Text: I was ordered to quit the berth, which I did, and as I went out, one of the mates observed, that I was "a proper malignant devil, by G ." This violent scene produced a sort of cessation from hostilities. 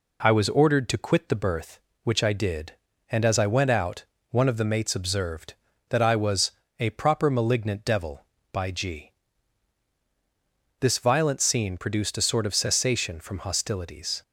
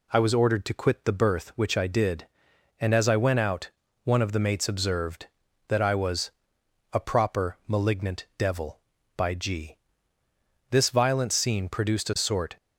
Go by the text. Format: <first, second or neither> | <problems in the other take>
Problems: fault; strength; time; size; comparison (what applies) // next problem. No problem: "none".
first | pauses between "was" and "a"; noticeable; at 6.3 s; 0.64 s long; slight in the first // stops before "of cessation from hostilities"; at 12.5 s